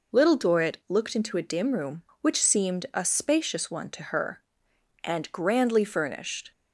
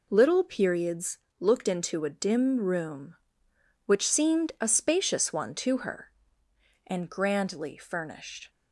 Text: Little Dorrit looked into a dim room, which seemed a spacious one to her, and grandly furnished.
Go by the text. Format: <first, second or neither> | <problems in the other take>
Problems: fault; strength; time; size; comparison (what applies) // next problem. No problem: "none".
first | says "Periods" for "Dorrit"; at 0.4 s